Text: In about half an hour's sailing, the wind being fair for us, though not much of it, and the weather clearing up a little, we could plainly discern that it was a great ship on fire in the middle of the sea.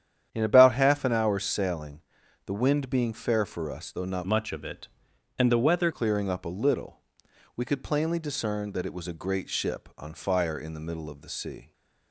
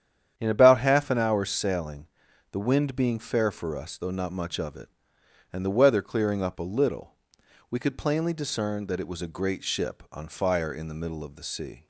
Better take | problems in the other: second | starts louder than the rest; strong; until 1.3 s; 9.5 dB; strong in the second // changes voice from "much" to "weather"; from 4.2 to 5.8 s; 1.6 s long

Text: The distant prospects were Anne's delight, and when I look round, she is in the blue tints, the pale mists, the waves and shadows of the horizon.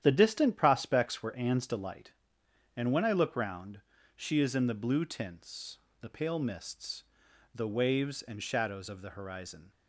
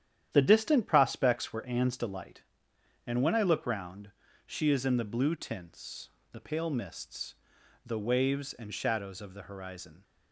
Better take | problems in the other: neither | starts louder than the rest; strong; the same in both

